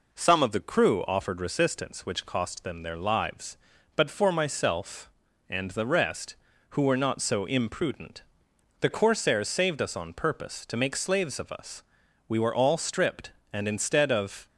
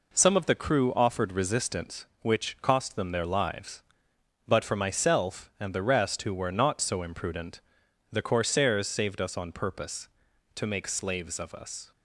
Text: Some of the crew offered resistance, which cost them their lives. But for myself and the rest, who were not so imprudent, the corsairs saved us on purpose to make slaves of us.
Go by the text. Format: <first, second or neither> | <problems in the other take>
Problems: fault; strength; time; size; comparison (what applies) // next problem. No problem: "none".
second | goes on to say "We were all stripped and instead of"; strong; from 12.2 s on; 2.2 s long